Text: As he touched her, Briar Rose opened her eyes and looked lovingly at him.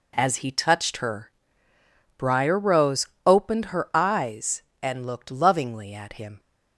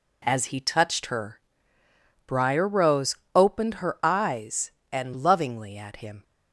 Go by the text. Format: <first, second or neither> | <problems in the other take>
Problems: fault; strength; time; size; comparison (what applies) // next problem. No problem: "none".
first | pauses between "Rose" and "opened"; slight; at 3.1 s; 0.20 s long; slight in the first // skips "looked"; at 5.1 s